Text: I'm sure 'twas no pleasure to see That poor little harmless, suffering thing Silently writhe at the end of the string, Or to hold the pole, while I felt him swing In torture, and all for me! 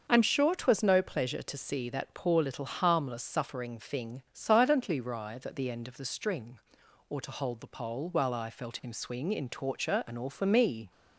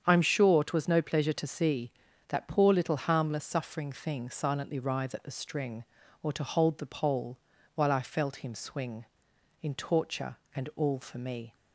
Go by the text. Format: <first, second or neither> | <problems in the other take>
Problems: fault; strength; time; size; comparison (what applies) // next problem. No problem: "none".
first | starts louder than the rest; strong; until 1.0 s; 8 dB; also in the first // skips "the end of"; at 5.2 s